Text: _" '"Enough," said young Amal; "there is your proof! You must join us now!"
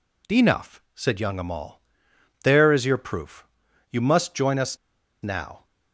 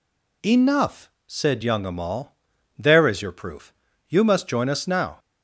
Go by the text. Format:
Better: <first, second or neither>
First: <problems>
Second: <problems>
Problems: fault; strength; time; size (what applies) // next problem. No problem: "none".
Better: second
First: pauses between "us" and "now"; noticeable; at 4.7 s; 0.46 s long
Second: none